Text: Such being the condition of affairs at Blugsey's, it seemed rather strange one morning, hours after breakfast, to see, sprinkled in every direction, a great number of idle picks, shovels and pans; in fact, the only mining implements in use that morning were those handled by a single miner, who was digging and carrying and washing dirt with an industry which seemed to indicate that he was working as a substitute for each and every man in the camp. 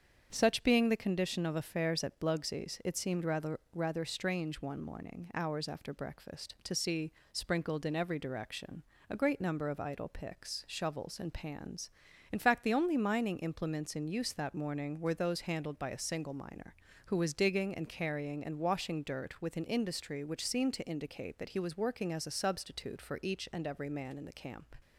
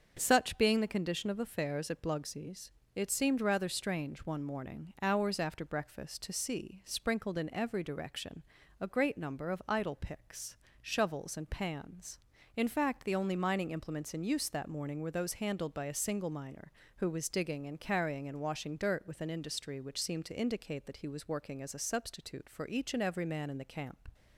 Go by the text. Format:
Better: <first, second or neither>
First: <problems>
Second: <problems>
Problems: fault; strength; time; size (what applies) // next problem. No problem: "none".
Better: second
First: starts louder than the rest; strong; until 1.3 s; 7.5 dB // says "rather" twice; at 3.7 s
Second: starts louder than the rest; until 1.1 s; 7 dB